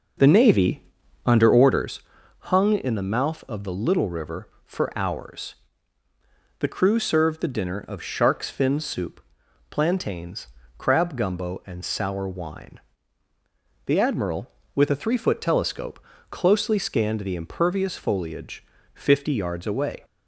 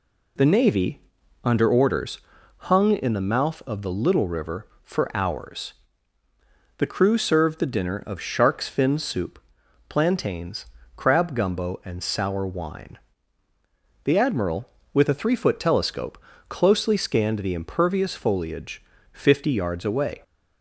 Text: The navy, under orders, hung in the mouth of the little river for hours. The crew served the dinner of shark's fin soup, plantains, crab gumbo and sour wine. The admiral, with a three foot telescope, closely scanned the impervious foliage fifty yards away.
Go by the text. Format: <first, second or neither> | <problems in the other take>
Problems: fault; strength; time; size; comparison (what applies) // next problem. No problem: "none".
second | starts louder than the rest; noticeable; until 1.9 s; 5.5 dB // pauses between "foliage" and "fifty"; slight; at 18.6 s; 0.28 s long; slight in the second